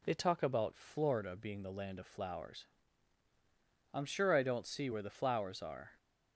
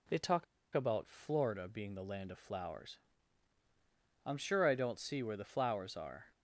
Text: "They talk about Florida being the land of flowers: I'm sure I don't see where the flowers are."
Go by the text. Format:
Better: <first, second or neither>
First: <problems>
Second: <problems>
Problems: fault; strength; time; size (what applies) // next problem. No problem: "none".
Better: first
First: none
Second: pauses between "talk" and "about"; slight; at 0.4 s; 0.30 s long